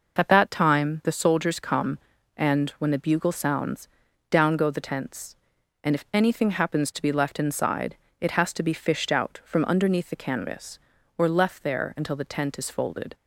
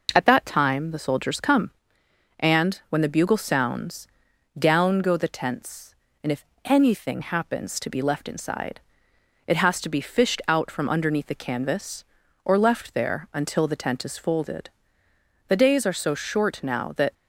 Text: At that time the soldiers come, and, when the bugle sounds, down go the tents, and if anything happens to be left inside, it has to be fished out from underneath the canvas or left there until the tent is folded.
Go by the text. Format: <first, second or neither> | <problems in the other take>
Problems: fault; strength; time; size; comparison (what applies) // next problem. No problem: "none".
first | pauses between "if" and "anything"; slight; at 6.4 s; 0.20 s long // goes on to say "The days are so short now that"; from 15.4 s on; 1.6 s long